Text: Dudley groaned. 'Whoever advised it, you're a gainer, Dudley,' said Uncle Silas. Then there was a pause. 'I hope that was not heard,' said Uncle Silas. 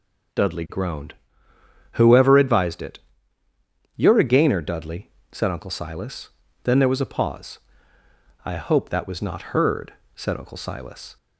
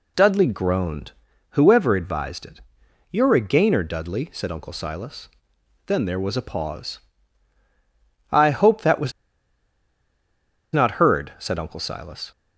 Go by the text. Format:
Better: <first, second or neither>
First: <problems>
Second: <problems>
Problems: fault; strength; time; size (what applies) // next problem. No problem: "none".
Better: first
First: none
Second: pauses between "was" and "not"; strong; at 9.1 s; 1.6 s long